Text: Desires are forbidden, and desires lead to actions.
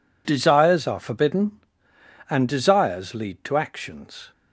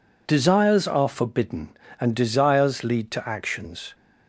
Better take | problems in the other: neither | none

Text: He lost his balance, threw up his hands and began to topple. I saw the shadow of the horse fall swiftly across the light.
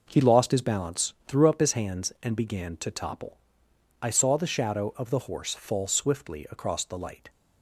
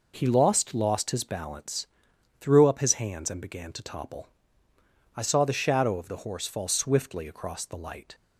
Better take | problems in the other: first | says "lost" twice; at 0.7 s

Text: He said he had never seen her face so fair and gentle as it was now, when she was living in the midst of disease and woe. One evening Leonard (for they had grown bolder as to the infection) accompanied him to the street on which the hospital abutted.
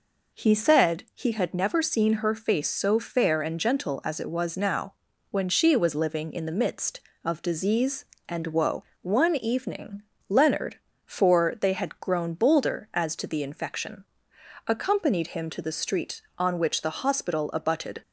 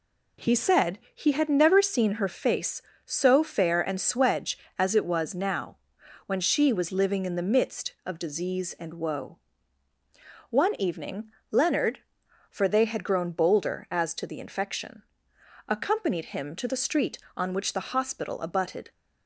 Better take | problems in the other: first | says "swedge" for "gentle"; at 3.9 s // pauses between "evening" and "Leonard"; slight; at 11.2 s; 0.22 s long; slight in the first

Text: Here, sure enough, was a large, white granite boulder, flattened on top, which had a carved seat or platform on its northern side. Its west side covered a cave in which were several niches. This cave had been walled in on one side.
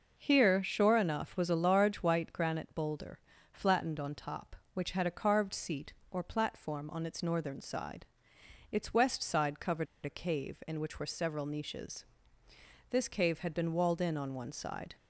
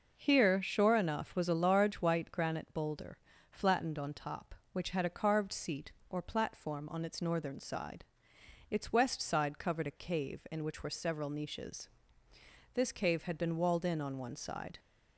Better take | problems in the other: second | pauses between "covered" and "a"; slight; at 9.8 s; 0.19 s long

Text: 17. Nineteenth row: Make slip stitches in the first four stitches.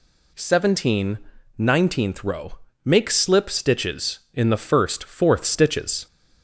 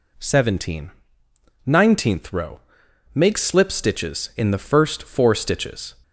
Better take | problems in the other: second | says "fourth" for "four"; at 5.0 s

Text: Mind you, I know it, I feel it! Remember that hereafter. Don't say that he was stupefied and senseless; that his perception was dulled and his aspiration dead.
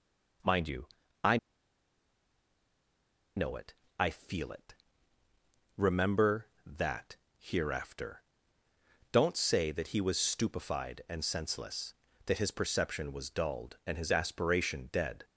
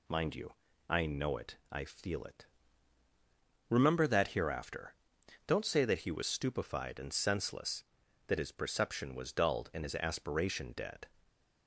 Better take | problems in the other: second | pauses between "I" and "know"; strong; at 1.3 s; 1.9 s long // pauses between "that" and "hereafter"; slight; at 7.1 s; 0.20 s long

